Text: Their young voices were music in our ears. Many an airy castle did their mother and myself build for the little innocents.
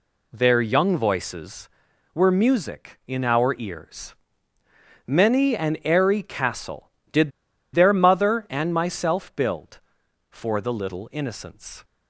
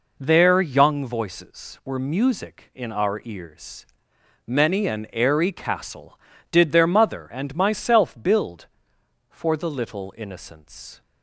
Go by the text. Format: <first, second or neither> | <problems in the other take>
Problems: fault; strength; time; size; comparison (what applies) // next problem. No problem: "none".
second | pauses between "did" and "their"; at 7.3 s; 0.43 s long